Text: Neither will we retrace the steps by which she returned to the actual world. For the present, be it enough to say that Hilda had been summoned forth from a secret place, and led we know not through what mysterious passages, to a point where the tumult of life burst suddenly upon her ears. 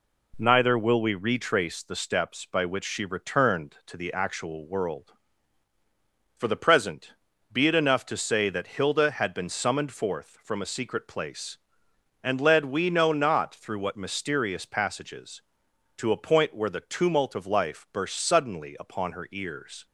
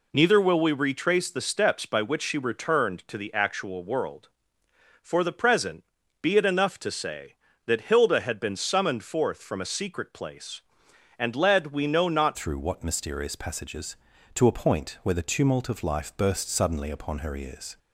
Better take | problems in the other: first | changes voice at "through"; from 12.3 s on; 5.4 s long

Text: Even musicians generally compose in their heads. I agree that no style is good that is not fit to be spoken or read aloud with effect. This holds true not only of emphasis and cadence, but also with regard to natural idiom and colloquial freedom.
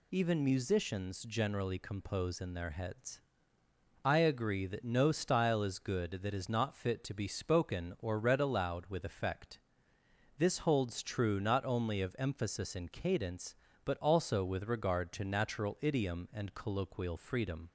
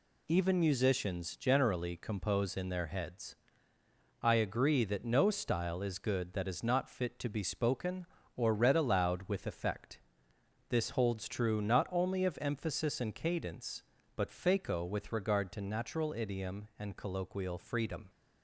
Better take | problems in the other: first | says "faco" for "also"; at 14.3 s

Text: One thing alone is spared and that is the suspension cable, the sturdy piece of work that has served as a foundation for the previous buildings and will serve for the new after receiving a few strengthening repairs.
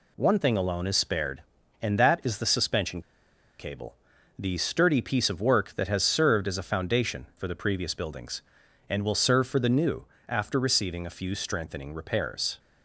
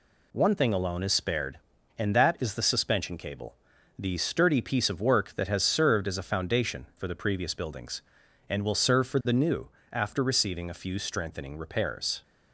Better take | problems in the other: second | pauses between "suspension" and "cable"; noticeable; at 2.9 s; 0.59 s long // pauses between "new" and "after"; slight; at 10.0 s; 0.24 s long; slight in the second

